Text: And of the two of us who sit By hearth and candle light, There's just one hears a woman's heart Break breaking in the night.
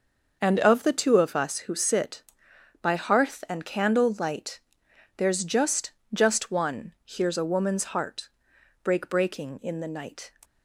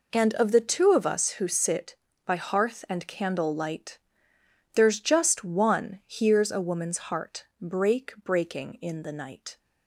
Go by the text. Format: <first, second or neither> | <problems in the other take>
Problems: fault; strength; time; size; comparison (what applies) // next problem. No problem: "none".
second | starts louder than the rest; noticeable; until 1.4 s; 6 dB // says "just" twice; at 6.1 s // pauses between "heart" and "Break"; noticeable; at 8.2 s; 0.54 s long; slight in the second